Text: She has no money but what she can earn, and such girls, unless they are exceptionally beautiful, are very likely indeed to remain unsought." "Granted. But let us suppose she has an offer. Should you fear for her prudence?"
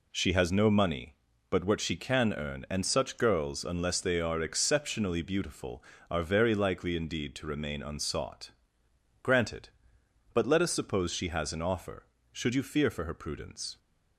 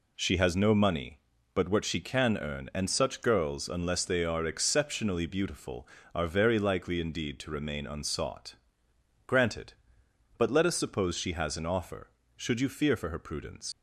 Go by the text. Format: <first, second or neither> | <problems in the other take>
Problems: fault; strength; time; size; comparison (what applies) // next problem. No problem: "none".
first | leaves "prudence" unfinished; at 13.7 s; 110 ms